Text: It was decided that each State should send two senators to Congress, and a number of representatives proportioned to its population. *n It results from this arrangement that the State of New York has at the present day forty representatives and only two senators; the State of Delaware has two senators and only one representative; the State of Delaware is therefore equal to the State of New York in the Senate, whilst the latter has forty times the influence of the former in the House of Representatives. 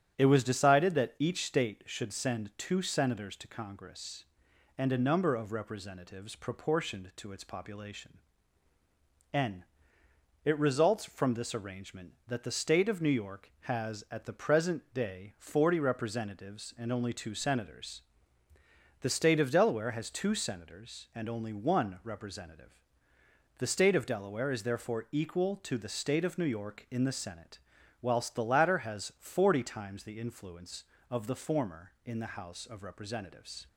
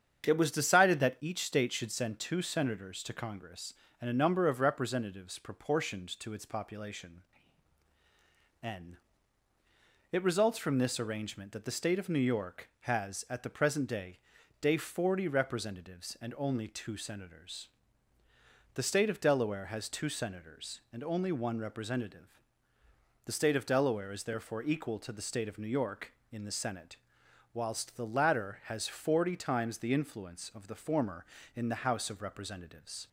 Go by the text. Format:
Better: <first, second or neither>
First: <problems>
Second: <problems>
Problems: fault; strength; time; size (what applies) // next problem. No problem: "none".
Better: first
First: starts louder than the rest; strong; until 1.2 s; 9 dB // pauses between "n" and "It"; noticeable; at 9.6 s; 0.80 s long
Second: starts louder than the rest; strong; until 1.3 s; 8 dB // pauses between "n" and "It"; at 8.9 s; 1.1 s long // says "day" twice; at 14.6 s